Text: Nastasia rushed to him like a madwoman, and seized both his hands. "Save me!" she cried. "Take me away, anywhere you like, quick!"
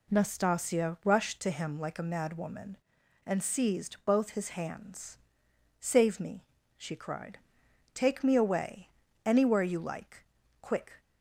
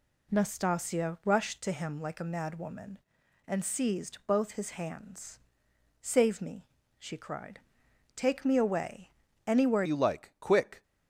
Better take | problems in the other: first | changes voice at "you"; from 9.8 s on; 1.0 s long

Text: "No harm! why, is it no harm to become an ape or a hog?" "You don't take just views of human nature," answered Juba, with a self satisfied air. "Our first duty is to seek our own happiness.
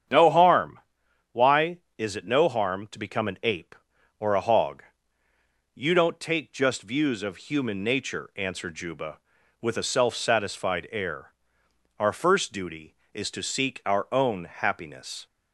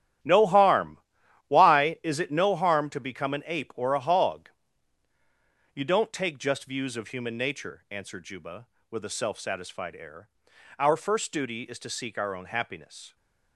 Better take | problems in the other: first | gets quieter; strong; throughout; 12.5 dB // starts louder than the rest; strong; until 1.7 s; 11.5 dB; strong in the first

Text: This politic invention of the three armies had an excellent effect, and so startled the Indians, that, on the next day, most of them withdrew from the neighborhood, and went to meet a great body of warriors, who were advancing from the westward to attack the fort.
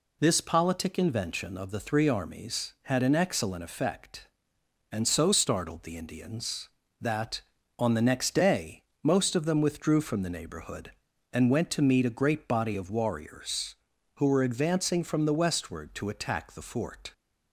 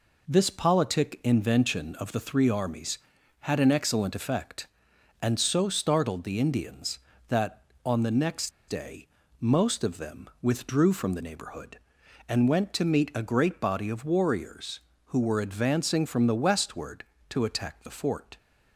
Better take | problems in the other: first | pauses between "next" and "day"; slight; at 8.4 s; 0.18 s long

